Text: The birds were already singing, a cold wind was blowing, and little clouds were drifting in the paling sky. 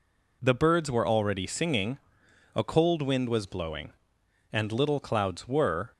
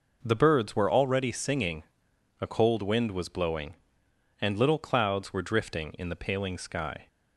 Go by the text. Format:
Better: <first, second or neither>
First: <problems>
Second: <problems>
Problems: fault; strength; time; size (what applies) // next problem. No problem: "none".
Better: second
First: stops before "drifting in the paling sky"; at 5.9 s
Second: none